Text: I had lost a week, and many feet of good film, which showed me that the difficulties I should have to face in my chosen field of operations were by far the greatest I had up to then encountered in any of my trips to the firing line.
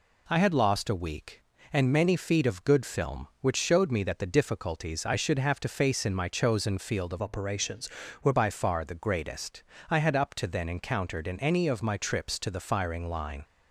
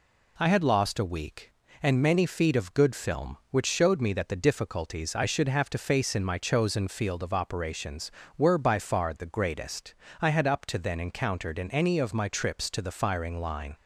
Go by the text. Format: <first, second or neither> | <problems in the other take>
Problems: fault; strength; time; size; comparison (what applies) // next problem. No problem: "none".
second | changes voice from "operations" to "were"; from 7.2 to 8.3 s; 1.1 s long // pauses between "greatest" and "I"; slight; at 9.6 s; 0.26 s long; slight in the second